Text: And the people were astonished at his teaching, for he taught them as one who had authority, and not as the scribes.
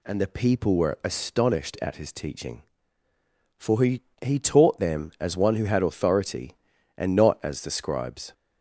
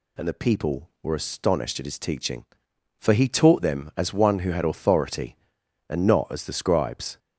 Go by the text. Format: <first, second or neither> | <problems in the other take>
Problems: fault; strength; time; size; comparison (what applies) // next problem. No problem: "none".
second | says "he" twice; at 4.2 s